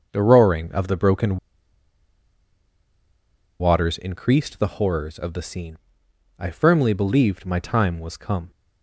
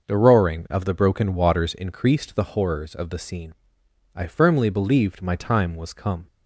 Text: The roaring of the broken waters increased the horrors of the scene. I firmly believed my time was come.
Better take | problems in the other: second | starts louder than the rest; noticeable; until 1.1 s; 6 dB; noticeable in the second // pauses between "broken" and "waters"; strong; at 1.3 s; 2.2 s long

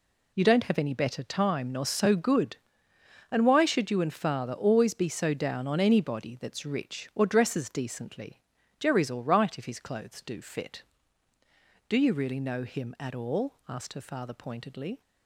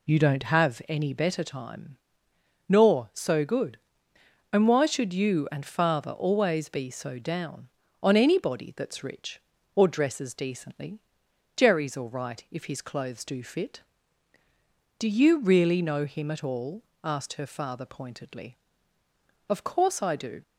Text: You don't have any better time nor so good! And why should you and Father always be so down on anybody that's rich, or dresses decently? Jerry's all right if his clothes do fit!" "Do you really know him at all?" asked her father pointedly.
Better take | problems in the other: first | pauses between "time" and "nor"; noticeable; at 1.9 s; 0.72 s long // goes on to say "Of course I do"; noticeable; from 19.4 s on; 0.94 s long

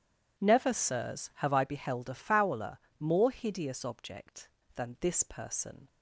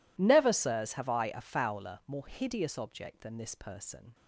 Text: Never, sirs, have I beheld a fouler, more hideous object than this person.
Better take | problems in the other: first | skips "beheld"; at 1.2 s

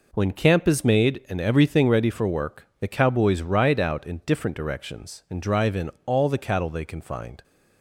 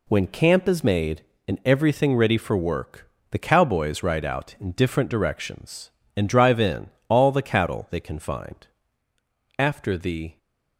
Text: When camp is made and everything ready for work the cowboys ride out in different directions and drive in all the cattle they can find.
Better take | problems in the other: first | pauses between "work" and "the"; slight; at 3.0 s; 0.20 s long // pauses between "in" and "all"; slight; at 6.8 s; 0.22 s long; slight in the first // goes on to say "After the"; noticeable; from 9.5 s on; 0.80 s long

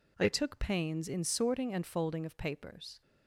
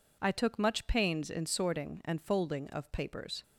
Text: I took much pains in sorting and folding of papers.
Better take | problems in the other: second | skips "much"; at 0.5 s

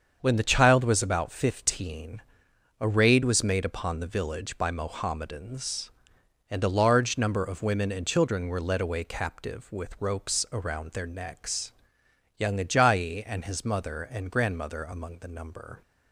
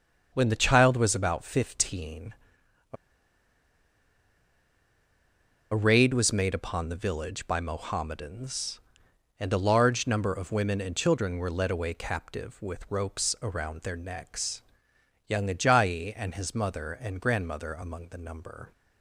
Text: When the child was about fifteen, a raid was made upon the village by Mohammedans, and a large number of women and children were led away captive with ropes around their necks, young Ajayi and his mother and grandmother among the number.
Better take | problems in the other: first | starts louder than the rest; until 1.3 s; 7 dB; also in the first // pauses between "a" and "raid"; strong; at 2.9 s; 2.7 s long

